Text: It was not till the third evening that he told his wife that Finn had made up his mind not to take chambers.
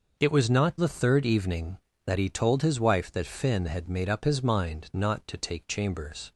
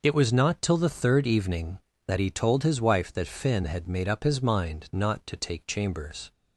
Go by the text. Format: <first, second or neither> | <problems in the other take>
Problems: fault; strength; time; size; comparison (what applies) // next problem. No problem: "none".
second | skips "till"; at 0.7 s